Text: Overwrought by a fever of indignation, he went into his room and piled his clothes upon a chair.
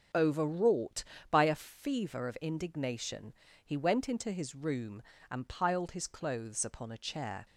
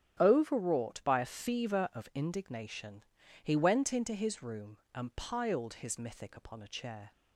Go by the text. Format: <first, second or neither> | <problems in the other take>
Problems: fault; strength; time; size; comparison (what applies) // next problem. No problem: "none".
first | starts louder than the rest; strong; until 1.2 s; 10.5 dB; also in the first // says "mythic" for "clothes"; at 5.9 s